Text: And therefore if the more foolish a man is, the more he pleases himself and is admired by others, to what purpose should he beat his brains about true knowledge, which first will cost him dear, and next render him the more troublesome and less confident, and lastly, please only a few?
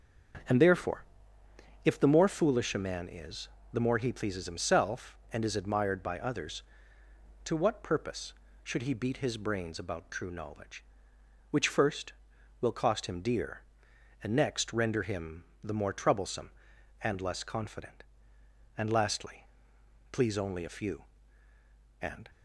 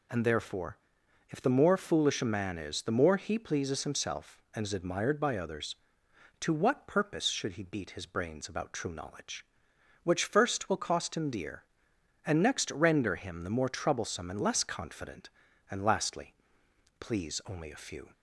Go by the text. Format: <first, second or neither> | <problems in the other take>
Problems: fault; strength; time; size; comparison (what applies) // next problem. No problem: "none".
second | starts louder than the rest; strong; until 2.2 s; 7.5 dB // pauses between "therefore" and "if"; noticeable; at 1.0 s; 0.80 s long; noticeable in the second // pauses between "him" and "the"; slight; at 15.4 s; 0.18 s long // goes on to say "And"; slight; from 22.0 s on; 0.28 s long